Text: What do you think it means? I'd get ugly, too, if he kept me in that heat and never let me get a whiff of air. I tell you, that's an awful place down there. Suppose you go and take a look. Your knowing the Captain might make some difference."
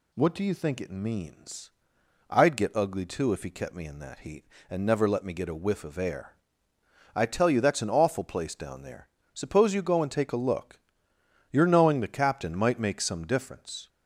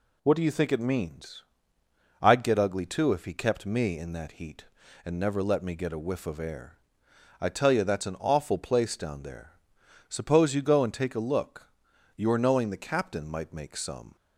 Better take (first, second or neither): first